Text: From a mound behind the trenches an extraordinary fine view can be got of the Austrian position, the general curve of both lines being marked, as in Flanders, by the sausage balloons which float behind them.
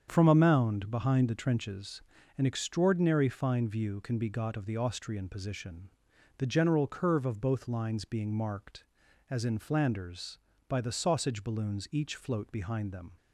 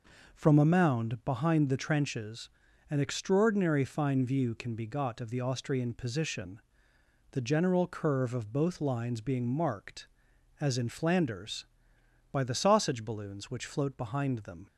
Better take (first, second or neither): second